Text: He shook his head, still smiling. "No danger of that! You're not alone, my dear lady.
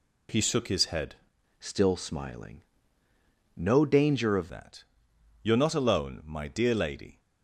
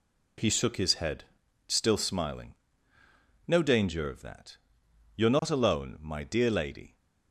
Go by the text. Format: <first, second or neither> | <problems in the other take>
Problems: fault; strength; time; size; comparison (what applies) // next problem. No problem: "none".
second | changes voice from "still" to "of"; from 1.6 to 4.5 s; 2.9 s long